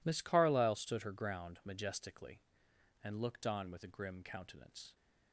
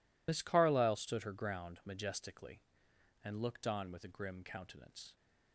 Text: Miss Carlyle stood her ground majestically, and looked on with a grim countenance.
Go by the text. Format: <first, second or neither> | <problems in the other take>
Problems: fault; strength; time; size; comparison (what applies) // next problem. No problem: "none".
first | loses the start of "Miss"; at 0.2 s; 60 ms